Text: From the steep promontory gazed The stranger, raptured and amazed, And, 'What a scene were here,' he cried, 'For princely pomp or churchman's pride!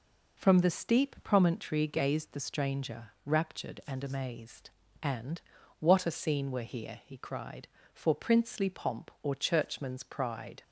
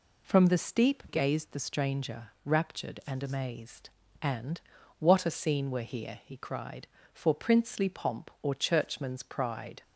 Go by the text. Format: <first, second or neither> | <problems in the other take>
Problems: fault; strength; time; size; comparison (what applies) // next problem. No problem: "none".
first | skips "promontory"; at 1.0 s